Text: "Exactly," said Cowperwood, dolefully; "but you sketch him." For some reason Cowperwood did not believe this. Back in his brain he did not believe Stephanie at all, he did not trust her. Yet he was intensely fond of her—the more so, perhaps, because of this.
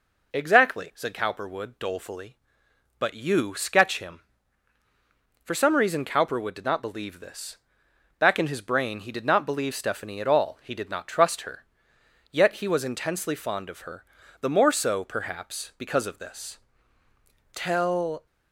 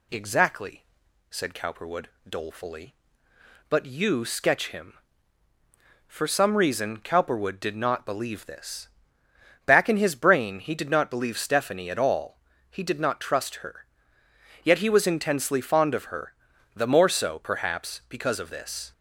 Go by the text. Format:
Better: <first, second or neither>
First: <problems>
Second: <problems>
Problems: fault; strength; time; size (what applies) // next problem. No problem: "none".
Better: second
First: goes on to say "Tell"; noticeable; from 17.5 s on; 0.72 s long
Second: none